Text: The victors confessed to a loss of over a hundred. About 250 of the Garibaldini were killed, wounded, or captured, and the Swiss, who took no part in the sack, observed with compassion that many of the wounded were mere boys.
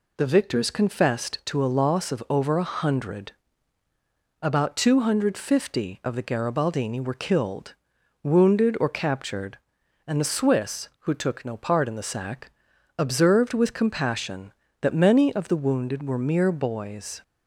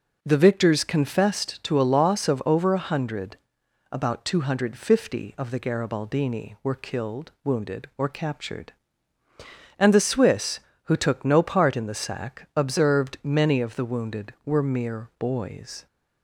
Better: first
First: none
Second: skips "with compassion that"; at 13.1 s

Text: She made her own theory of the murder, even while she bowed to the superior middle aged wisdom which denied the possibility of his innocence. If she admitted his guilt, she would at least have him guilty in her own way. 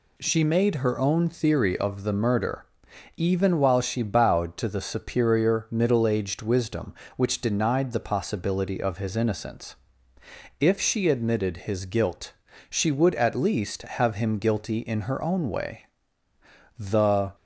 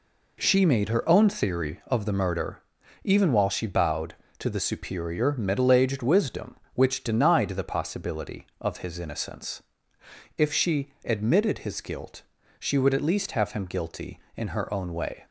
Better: second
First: goes on to say "The"; from 16.7 s on; 0.56 s long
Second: none

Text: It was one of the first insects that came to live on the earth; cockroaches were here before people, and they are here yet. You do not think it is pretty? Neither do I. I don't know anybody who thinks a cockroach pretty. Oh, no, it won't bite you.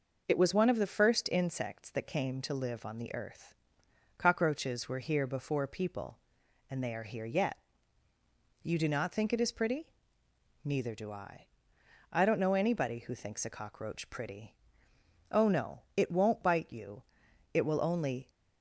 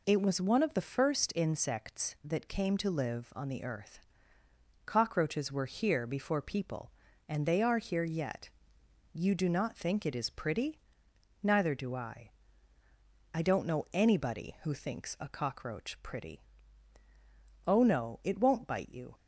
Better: second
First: goes on to say "It will only"; noticeable; from 17.5 s on; 0.78 s long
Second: none

